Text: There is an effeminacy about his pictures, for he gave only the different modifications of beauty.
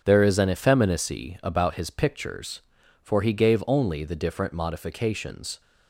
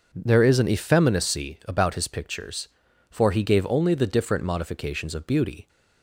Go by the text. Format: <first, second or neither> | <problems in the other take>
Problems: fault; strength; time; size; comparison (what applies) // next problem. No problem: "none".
second | starts louder than the rest; strong; until 1.0 s; 8 dB; noticeable in the second // stops before "of beauty"; at 5.6 s